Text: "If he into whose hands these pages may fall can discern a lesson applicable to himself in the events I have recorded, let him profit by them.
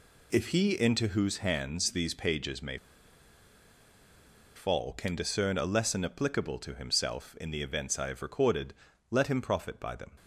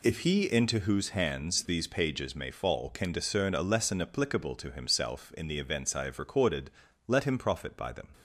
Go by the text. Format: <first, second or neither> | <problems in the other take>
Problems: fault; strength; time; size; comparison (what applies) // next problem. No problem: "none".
second | pauses between "may" and "fall"; strong; at 2.7 s; 1.7 s long